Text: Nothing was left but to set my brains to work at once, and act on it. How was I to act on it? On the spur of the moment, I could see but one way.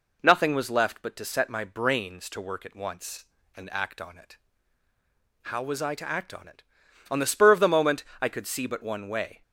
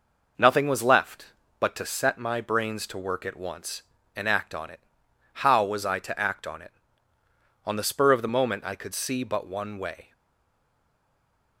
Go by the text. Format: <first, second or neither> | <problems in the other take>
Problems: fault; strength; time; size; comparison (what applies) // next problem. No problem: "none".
first | stays silent after the last word; noticeable; from 10.1 s on; 1.4 s long